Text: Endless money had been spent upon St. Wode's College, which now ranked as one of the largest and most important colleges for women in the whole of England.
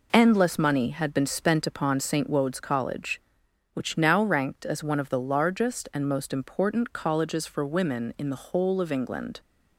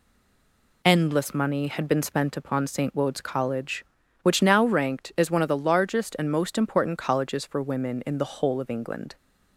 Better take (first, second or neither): first